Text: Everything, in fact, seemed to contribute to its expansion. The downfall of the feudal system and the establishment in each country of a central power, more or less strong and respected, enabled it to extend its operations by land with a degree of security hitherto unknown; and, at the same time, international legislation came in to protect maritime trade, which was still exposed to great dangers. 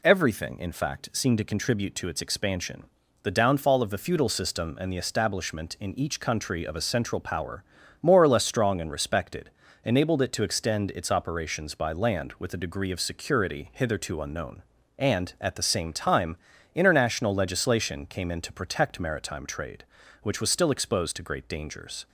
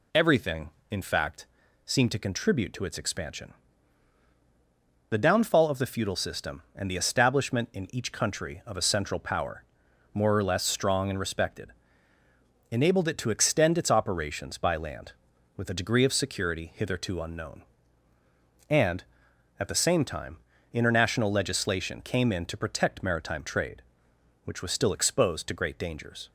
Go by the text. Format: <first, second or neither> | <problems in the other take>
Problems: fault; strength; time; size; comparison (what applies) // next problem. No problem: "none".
neither | none